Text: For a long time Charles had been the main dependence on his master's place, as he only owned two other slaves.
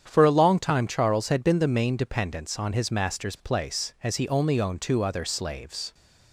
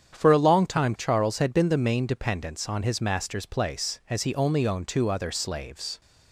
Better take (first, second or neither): neither